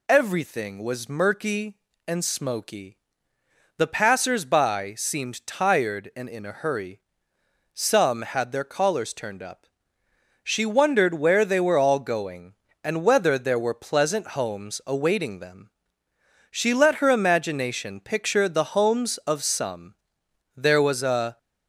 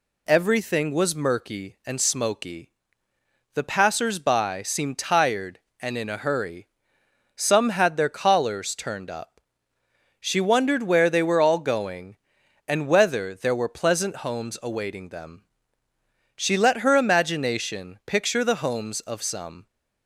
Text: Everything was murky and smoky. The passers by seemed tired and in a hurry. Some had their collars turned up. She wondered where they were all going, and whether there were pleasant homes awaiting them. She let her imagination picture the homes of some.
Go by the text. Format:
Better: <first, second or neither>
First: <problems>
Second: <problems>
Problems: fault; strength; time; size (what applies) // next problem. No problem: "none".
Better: second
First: goes on to say "There was a"; noticeable; from 20.5 s on; 0.82 s long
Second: none